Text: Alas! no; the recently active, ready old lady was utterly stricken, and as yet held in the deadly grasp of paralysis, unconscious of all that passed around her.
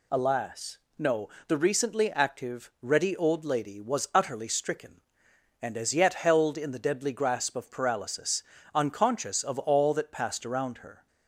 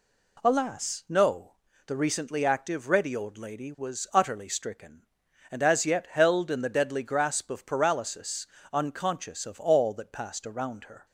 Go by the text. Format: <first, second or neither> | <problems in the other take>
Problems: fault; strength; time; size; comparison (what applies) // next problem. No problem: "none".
neither | none